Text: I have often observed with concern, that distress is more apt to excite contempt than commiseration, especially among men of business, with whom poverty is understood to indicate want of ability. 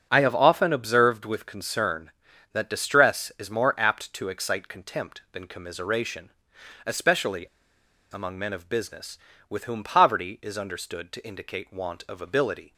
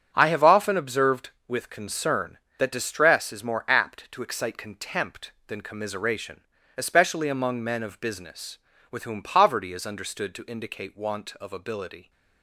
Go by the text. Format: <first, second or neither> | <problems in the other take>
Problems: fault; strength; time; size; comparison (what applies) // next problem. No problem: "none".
second | starts louder than the rest; until 1.1 s; 6.5 dB; strong in the second // pauses between "especially" and "among"; noticeable; at 7.4 s; 0.68 s long